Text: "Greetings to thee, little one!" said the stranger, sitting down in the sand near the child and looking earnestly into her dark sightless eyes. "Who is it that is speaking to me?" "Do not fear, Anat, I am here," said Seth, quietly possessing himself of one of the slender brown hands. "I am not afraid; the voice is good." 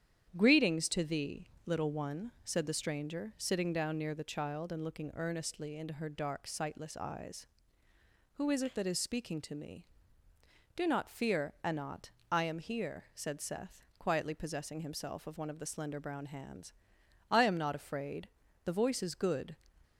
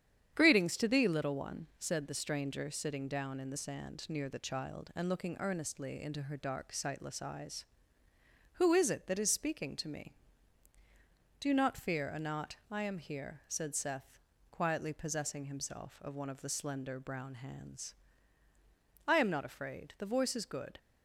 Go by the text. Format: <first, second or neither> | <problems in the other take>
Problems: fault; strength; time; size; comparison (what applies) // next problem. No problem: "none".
second | starts louder than the rest; strong; until 1.3 s; 9 dB; strong in the second // skips "in the sand"; at 3.9 s